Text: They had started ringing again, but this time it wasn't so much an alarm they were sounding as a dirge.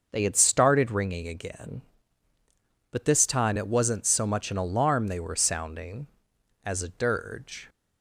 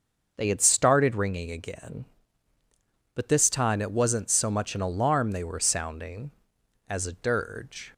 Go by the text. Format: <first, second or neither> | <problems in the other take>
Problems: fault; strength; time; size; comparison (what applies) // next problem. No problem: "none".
neither | starts louder than the rest; the same in both